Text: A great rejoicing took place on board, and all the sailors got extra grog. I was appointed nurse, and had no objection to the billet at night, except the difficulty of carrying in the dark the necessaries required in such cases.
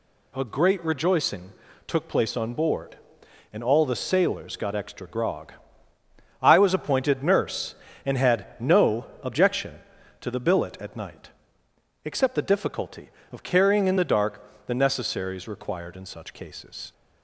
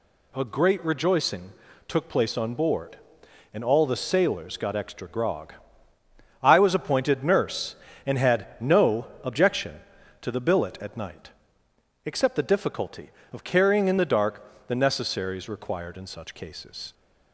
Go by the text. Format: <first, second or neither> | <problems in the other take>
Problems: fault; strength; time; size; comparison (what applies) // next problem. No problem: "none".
neither | pauses between "rejoicing" and "took"; slight; the same in both // pauses between "no" and "objection"; slight; the same in both // pauses between "dark" and "the"; slight; the same in both